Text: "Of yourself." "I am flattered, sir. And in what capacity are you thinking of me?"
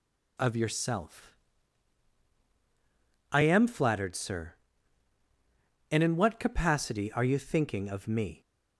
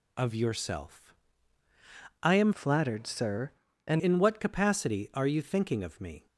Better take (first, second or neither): first